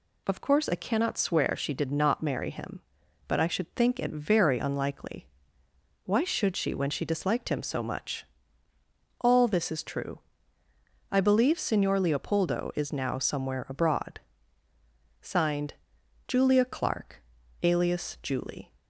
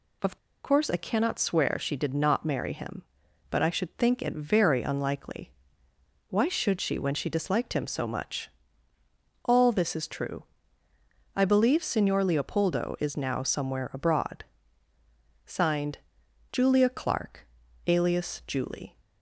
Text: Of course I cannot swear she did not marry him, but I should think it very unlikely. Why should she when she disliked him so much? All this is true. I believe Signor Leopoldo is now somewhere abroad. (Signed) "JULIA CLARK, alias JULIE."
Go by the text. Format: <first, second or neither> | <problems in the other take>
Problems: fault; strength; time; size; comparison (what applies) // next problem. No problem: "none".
first | pauses between "Of" and "course"; slight; at 0.3 s; 0.28 s long